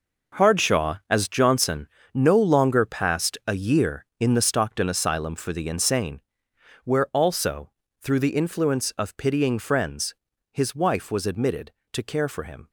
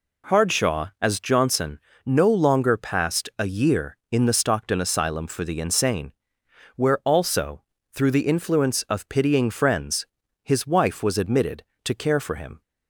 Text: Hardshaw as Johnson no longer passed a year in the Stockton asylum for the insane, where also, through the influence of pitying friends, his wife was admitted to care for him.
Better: second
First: gets quieter; strong; throughout; 11 dB // pauses between "Johnson" and "no"; slight; at 1.8 s; 0.24 s long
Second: pauses between "Johnson" and "no"; slight; at 1.7 s; 0.24 s long

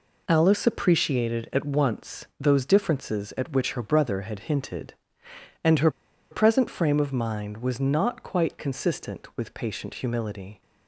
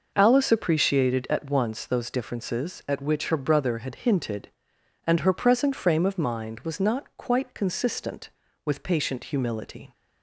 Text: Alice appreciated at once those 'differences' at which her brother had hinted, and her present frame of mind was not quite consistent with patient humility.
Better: second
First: pauses between "her" and "present"; at 5.8 s; 0.40 s long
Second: none

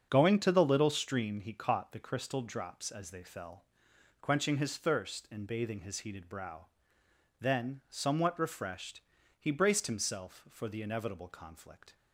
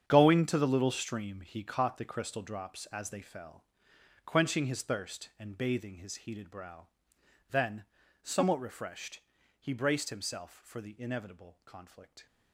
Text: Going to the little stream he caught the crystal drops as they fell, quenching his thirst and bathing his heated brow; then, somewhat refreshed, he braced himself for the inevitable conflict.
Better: first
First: starts louder than the rest; until 1.1 s; 7 dB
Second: gets quieter; strong; throughout; 13.5 dB // starts louder than the rest; strong; until 1.0 s; 8.5 dB

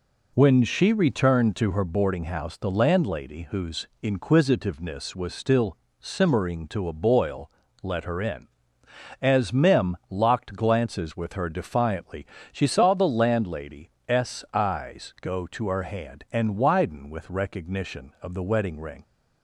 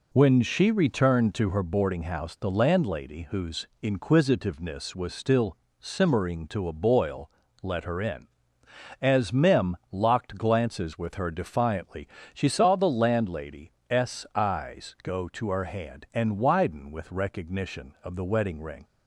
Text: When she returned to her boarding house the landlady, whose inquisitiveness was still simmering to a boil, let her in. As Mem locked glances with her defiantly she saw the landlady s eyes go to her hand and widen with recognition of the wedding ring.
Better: neither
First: pauses between "whose" and "inquisitiveness"; slight; at 3.8 s; 0.16 s long // pauses between "still" and "simmering"; slight; at 5.7 s; 0.24 s long // pauses between "defiantly" and "she"; slight; at 12.2 s; 0.26 s long // pauses between "landlady" and "s"; slight; at 13.9 s; 0.18 s long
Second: pauses between "whose" and "inquisitiveness"; slight; at 3.6 s; 0.16 s long // pauses between "still" and "simmering"; slight; at 5.5 s; 0.24 s long // pauses between "defiantly" and "she"; slight; at 12.0 s; 0.26 s long // pauses between "landlady" and "s"; slight; at 13.7 s; 0.18 s long

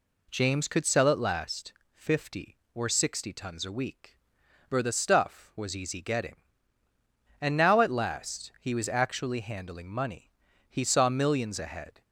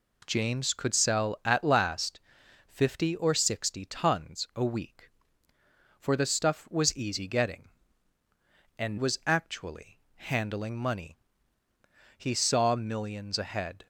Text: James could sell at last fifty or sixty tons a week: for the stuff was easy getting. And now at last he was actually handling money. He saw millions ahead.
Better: first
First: pauses between "last" and "fifty"; slight; at 1.7 s; 0.20 s long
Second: pauses between "last" and "fifty"; noticeable; at 2.2 s; 0.48 s long // skips "now at last he"; at 8.9 s // pauses between "actually" and "handling"; slight; at 9.9 s; 0.16 s long

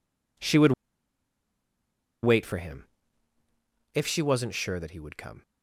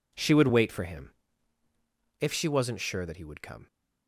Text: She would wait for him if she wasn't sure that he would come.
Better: second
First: pauses between "would" and "wait"; strong; at 0.7 s; 1.5 s long // pauses between "him" and "if"; at 2.8 s; 1.0 s long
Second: pauses between "him" and "if"; at 1.1 s; 1.0 s long

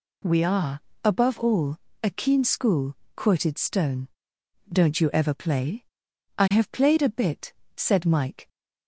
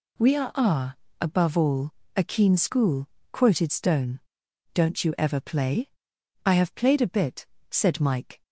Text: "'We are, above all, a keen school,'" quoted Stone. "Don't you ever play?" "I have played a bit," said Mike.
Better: first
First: none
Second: says "are" twice; at 0.5 s

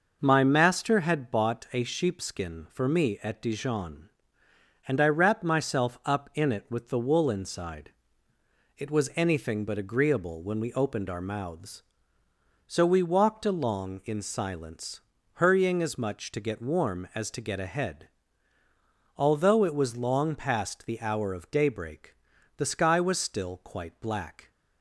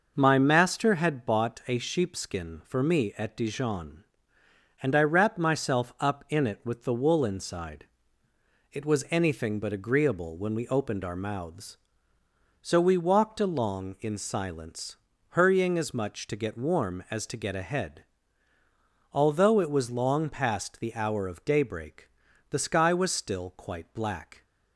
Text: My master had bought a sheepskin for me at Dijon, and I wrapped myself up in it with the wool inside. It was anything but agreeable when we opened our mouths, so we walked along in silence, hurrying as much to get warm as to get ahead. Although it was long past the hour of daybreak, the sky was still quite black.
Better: neither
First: none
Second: none

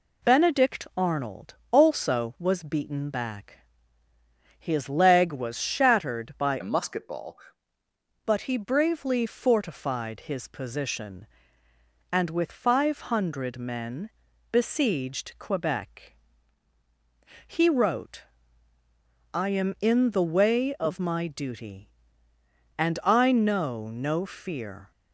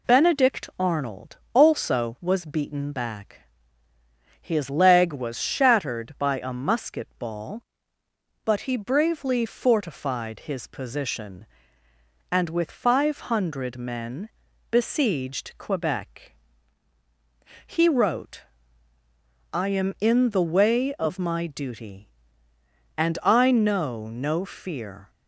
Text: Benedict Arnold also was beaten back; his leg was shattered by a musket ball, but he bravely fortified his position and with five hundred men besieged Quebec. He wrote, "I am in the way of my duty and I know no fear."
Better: second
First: pauses between "Arnold" and "also"; slight; at 1.5 s; 0.16 s long // changes voice from "a" to "ball"; from 6.6 to 7.3 s; 0.7 s long // pauses between "men" and "besieged"; at 14.0 s; 0.44 s long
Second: pauses between "Arnold" and "also"; slight; at 1.3 s; 0.16 s long // pauses between "men" and "besieged"; at 14.2 s; 0.44 s long

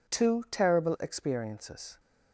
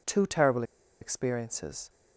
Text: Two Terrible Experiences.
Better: first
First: none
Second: pauses between "Terrible" and "Experiences"; at 0.6 s; 0.37 s long

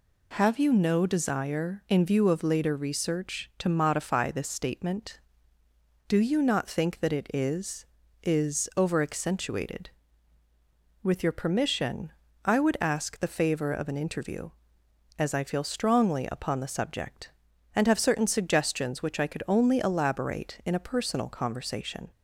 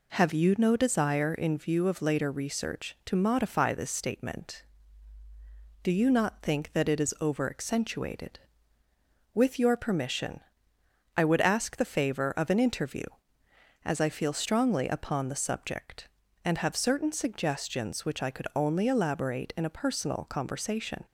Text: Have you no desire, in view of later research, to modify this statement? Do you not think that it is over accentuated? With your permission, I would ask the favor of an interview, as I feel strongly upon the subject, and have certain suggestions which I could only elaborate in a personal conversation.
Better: second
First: says "is" twice; at 8.2 s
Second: none

